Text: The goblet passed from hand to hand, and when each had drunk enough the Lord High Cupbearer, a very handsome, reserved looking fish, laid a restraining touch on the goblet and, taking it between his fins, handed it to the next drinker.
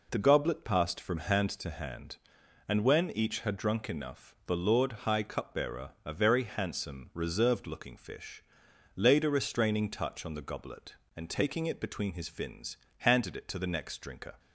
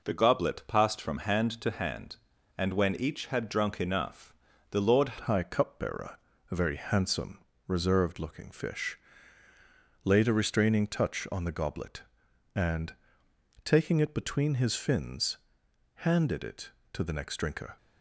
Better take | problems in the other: first | pauses between "enough" and "the"; slight; at 4.3 s; 0.36 s long // changes voice at "High"; from 5.2 s on; 12.5 s long

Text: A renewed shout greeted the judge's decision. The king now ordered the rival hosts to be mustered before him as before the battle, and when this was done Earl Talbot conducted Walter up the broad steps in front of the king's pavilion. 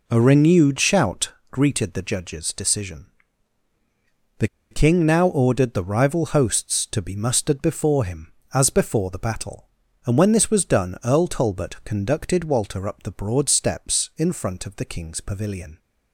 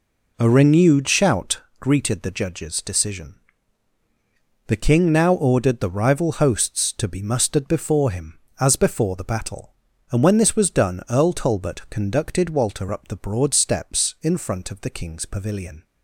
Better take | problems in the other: second | pauses between "shout" and "greeted"; slight; at 1.3 s; 0.18 s long; slight in the second // pauses between "The" and "king"; slight; at 4.4 s; 0.25 s long

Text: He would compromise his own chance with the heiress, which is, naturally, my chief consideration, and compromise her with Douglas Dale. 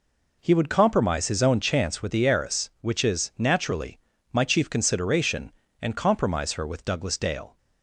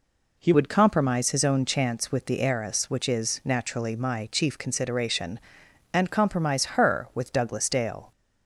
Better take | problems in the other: first | changes voice at "would"; from 0.5 s on; 7.6 s long

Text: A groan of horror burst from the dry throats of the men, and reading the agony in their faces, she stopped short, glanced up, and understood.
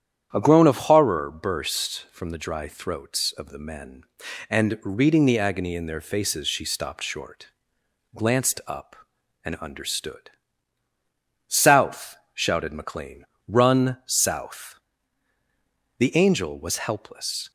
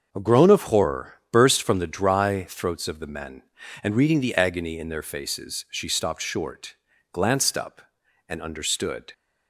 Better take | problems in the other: second | starts louder than the rest; strong; until 1.3 s; 9.5 dB; also in the second // goes on to say "South shouted McLean Run south The Angel was helpless"; strong; from 11.4 s on; 6.0 s long

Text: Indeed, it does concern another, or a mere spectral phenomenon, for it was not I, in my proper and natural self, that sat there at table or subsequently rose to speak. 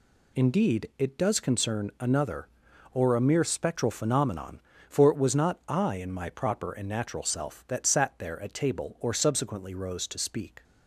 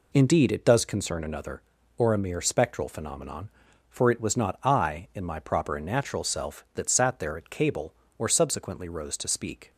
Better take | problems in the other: first | says "cable" for "table"; at 7.4 s

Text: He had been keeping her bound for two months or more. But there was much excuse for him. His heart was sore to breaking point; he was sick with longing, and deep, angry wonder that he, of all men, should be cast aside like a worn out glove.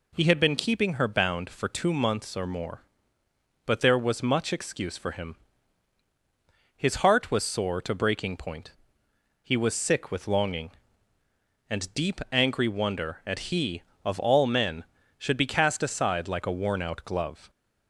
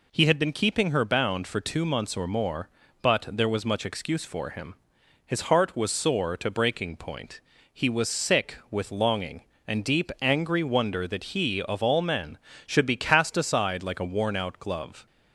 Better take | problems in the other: second | says "at" for "that"; at 13.2 s

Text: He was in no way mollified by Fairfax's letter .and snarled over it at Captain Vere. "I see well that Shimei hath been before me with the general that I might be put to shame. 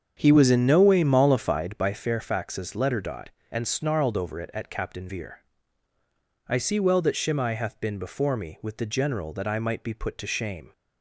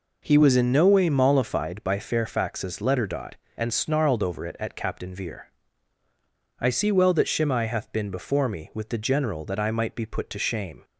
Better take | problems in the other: second | starts louder than the rest; strong; until 2.0 s; 7.5 dB

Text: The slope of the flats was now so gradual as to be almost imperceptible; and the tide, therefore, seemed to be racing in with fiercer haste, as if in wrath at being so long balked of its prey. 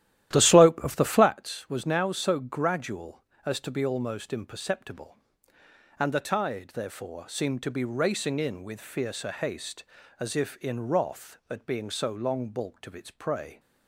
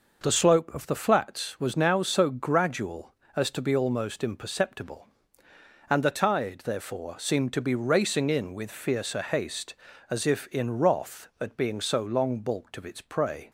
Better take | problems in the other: second | starts louder than the rest; strong; until 1.3 s; 13 dB

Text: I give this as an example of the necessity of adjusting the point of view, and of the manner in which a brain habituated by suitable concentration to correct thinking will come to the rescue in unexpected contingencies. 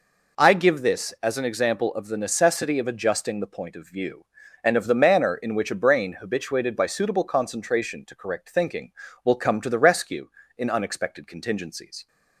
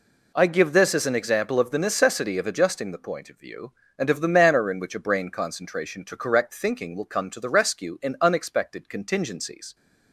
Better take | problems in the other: first | skips "habituated by suitable"; at 5.2 s

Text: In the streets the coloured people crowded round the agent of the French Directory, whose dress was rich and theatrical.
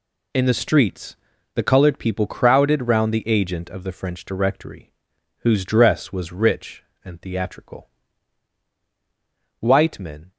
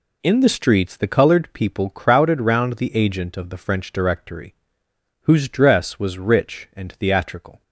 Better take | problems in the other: second | pauses between "streets" and "the"; at 1.1 s; 0.38 s long // goes on to say "White men"; noticeable; from 9.5 s on; 0.72 s long

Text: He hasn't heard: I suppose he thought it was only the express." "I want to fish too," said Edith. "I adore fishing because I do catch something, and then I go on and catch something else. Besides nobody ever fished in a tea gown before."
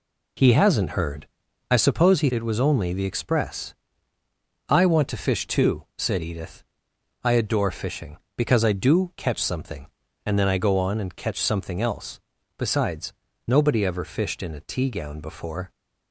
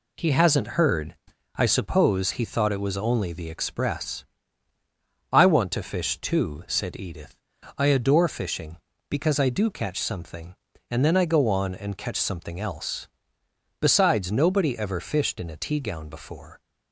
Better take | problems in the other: second | skips "thought"; at 2.3 s // pauses between "Besides" and "nobody"; slight; at 13.1 s; 0.32 s long

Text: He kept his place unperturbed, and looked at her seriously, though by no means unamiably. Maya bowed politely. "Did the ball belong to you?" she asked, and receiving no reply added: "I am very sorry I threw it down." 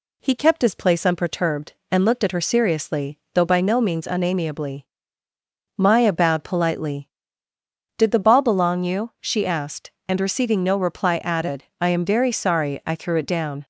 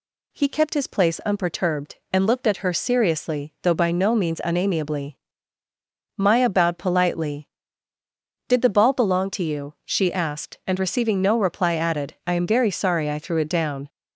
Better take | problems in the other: second | skips "to"; at 8.8 s

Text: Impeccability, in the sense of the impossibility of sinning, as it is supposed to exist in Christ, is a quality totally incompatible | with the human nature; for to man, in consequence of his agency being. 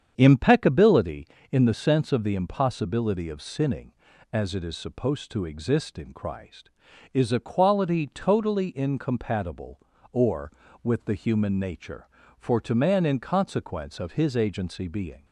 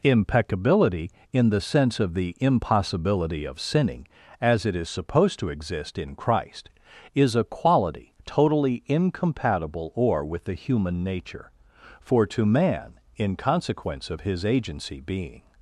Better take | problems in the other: second | starts louder than the rest; strong; until 1.5 s; 8 dB

